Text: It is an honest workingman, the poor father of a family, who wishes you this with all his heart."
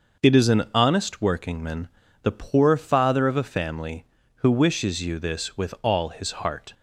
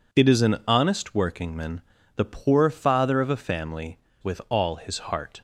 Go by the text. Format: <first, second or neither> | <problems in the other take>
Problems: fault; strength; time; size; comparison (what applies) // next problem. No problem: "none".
first | skips "who wishes you this"; at 4.1 s